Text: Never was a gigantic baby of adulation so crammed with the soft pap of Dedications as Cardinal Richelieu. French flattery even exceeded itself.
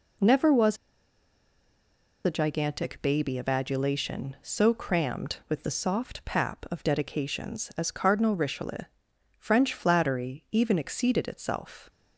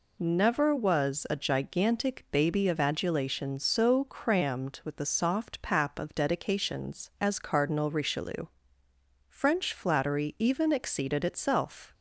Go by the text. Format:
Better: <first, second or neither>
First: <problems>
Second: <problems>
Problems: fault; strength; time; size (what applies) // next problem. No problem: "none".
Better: second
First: pauses between "was" and "a"; strong; at 0.7 s; 1.4 s long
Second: none